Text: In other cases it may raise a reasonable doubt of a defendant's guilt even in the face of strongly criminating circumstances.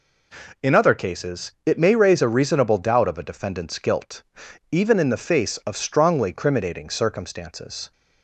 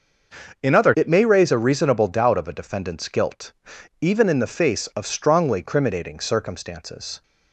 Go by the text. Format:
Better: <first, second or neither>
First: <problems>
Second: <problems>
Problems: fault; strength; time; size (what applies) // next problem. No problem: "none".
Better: first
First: pauses between "guilt" and "even"; noticeable; at 4.2 s; 0.50 s long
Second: starts louder than the rest; noticeable; until 1.6 s; 6 dB // skips "cases"; at 0.9 s // pauses between "guilt" and "even"; noticeable; at 3.5 s; 0.50 s long